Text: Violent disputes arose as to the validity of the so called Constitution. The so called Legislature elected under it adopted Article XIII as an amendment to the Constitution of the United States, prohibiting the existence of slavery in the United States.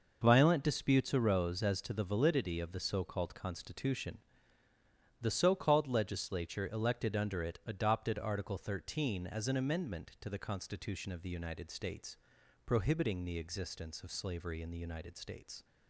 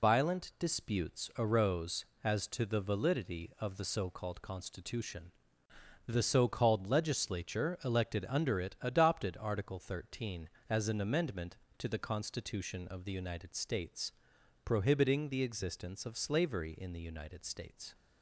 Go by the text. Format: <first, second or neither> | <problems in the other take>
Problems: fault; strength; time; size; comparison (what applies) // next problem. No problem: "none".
first | loses the start of "Violent"; at 0.0 s; 115 ms